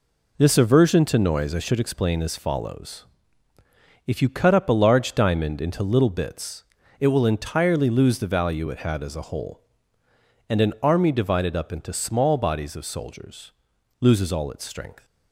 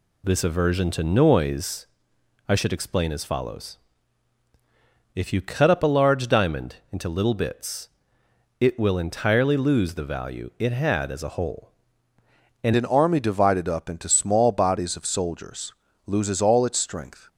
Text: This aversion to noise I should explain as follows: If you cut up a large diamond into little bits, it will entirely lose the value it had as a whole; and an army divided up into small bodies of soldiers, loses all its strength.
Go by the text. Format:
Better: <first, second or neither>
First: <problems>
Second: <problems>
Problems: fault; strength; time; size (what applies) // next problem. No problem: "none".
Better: first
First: none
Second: pauses between "noise" and "I"; noticeable; at 1.8 s; 0.64 s long // changes voice at "an"; from 12.7 s on; 4.5 s long